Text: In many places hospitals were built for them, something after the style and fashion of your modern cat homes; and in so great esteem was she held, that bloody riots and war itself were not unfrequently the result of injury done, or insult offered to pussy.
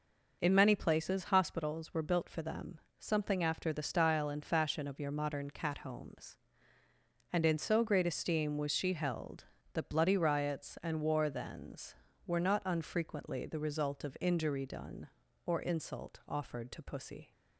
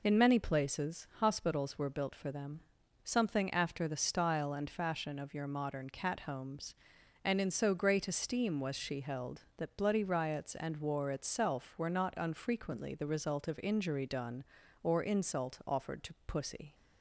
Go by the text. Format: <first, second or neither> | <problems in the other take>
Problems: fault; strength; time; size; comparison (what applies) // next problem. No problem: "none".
second | says "thens" for "itself"; at 11.2 s